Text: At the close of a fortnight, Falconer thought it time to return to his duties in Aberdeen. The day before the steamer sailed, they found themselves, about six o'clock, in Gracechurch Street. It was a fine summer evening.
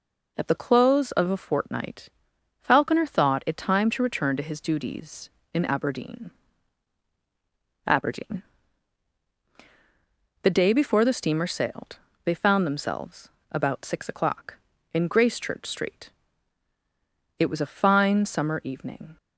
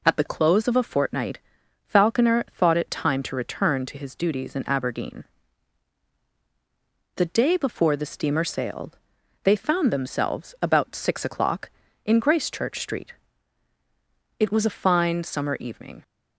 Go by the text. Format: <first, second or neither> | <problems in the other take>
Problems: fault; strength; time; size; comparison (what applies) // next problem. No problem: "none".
second | says "Aberdeen" twice; at 7.8 s